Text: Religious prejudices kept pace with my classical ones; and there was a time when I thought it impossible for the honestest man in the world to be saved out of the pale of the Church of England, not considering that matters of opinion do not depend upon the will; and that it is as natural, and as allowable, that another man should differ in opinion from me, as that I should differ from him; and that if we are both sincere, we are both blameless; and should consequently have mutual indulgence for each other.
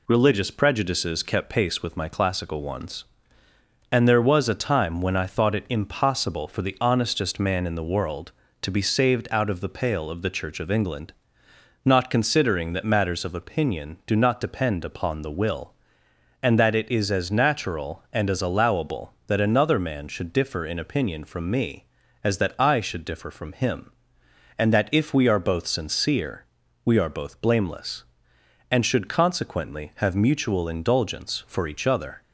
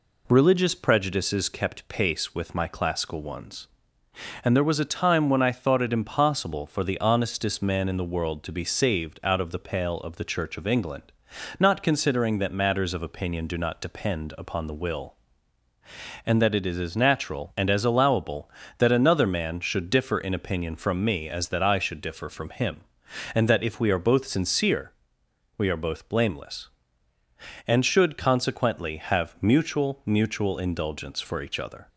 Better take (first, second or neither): first